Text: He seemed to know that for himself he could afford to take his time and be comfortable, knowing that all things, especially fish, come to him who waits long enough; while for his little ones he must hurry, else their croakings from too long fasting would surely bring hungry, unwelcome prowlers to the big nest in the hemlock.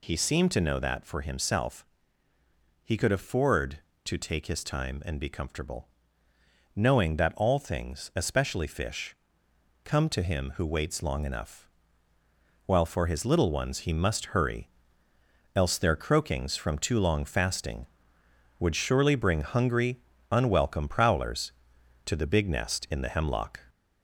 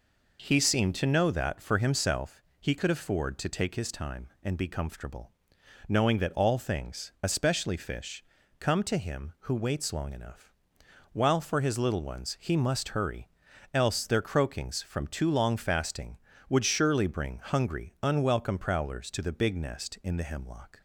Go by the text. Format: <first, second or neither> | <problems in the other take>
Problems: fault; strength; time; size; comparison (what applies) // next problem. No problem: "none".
second | gets louder; slight; throughout; 3 dB // pauses between "himself" and "he"; noticeable; at 1.8 s; 0.98 s long; slight in the second